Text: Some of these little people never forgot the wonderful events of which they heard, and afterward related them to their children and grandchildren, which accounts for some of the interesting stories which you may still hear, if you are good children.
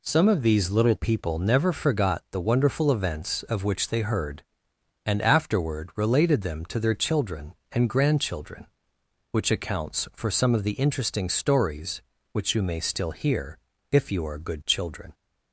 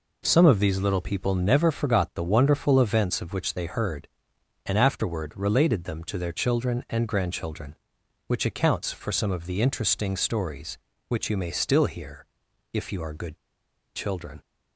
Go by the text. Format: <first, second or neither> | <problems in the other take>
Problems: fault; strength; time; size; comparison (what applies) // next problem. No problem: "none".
first | pauses between "good" and "children"; noticeable; at 13.3 s; 0.56 s long